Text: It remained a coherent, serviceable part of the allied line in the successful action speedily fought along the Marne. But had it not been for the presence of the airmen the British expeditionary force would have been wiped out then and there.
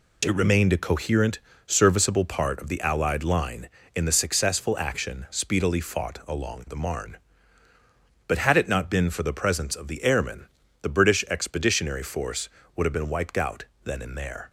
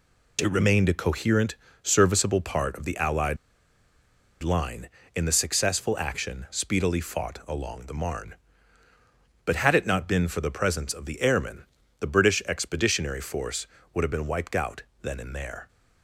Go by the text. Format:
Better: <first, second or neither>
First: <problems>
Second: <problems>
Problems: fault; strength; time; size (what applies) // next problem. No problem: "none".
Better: first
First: pauses between "airmen" and "the"; slight; at 10.4 s; 0.36 s long // pauses between "out" and "then"; slight; at 13.6 s; 0.18 s long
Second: pauses between "allied" and "line"; at 3.3 s; 1.0 s long // pauses between "airmen" and "the"; slight; at 11.6 s; 0.36 s long // pauses between "out" and "then"; slight; at 14.8 s; 0.18 s long